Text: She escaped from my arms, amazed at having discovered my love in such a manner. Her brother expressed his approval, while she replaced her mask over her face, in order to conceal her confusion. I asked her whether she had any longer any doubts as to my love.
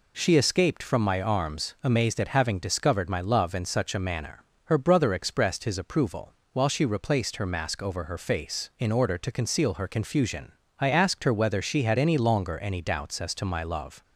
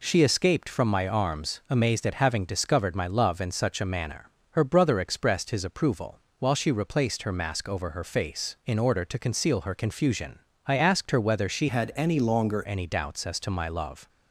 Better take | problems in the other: first | changes voice from "had" to "longer"; from 11.6 to 12.6 s; 1.0 s long

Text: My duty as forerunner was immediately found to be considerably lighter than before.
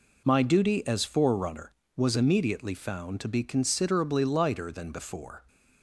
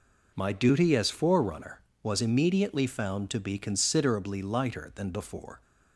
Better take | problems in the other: neither | none

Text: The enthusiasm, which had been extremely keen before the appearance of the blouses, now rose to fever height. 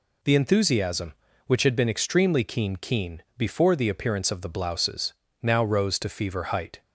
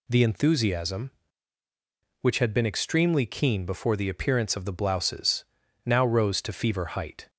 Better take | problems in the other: second | says "keen" twice; at 2.7 s

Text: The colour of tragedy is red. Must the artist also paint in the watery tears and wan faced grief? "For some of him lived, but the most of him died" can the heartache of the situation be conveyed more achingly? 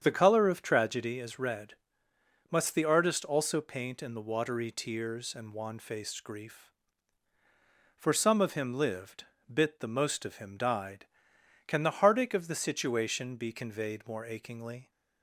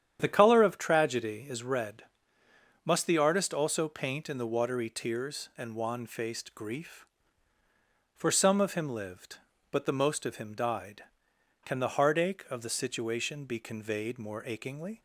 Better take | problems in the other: second | starts louder than the rest; strong; until 1.0 s; 8 dB; strong in the second // says "bit" for "but"; at 9.5 s

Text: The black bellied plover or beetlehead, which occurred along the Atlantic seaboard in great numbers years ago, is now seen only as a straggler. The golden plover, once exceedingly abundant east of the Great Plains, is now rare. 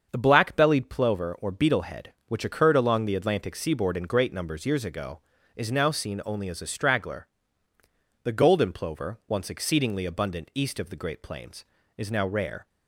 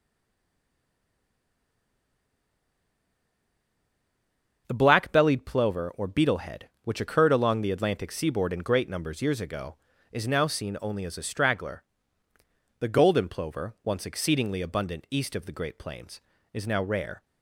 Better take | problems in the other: first | stays silent before the first word; strong; until 4.6 s; 4.6 s long // starts louder than the rest; until 5.6 s; 7 dB; also in the first

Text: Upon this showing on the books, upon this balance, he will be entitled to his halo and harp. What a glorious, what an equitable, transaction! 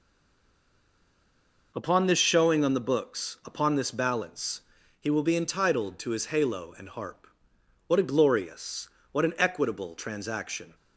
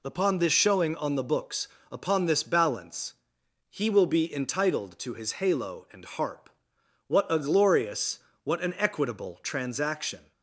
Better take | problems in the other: second | stays silent before the first word; noticeable; until 1.7 s; 1.7 s long

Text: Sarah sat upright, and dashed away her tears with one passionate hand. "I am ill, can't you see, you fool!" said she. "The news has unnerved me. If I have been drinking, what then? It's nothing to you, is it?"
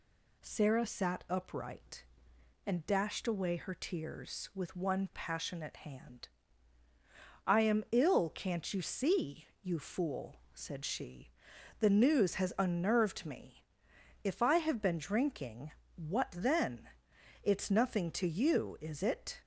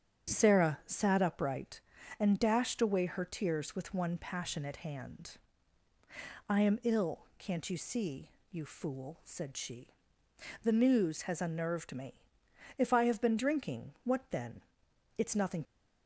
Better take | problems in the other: first | starts louder than the rest; strong; until 1.3 s; 8 dB // stops before "to you is it"; at 15.6 s

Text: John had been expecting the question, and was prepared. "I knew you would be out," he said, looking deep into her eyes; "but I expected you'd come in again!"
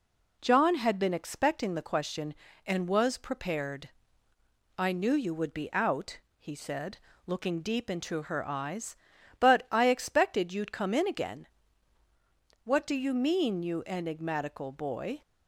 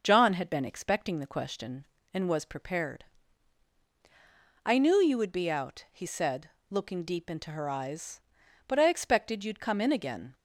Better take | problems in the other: second | goes on to say "What do you mean you enigmatical boy"; strong; from 12.6 s on; 2.5 s long

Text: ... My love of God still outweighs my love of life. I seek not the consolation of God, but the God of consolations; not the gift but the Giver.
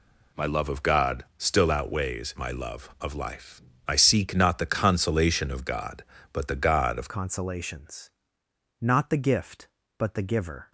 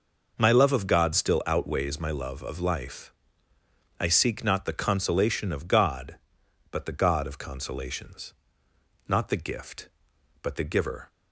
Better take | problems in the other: second | changes voice at "consolations"; from 7.0 s on; 3.7 s long

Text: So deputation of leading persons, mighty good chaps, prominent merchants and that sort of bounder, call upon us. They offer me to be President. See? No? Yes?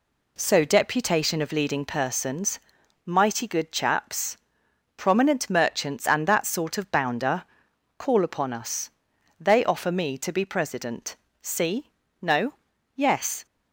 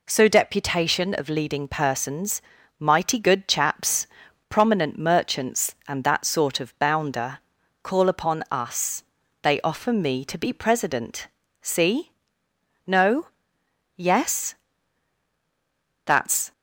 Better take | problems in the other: first | goes on to say "That's"; slight; from 16.0 s on; 0.46 s long

